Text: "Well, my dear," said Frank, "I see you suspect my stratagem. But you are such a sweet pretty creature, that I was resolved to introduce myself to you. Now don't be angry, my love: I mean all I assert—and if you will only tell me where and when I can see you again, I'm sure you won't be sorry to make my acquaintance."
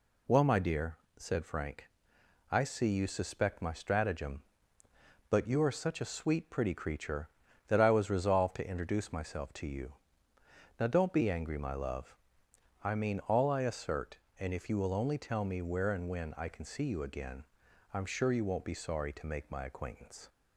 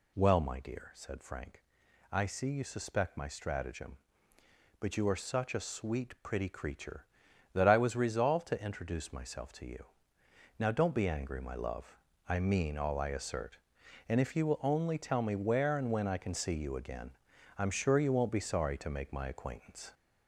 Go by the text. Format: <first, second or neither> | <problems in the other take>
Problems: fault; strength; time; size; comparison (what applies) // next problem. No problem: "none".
first | gets louder; noticeable; throughout; 4.5 dB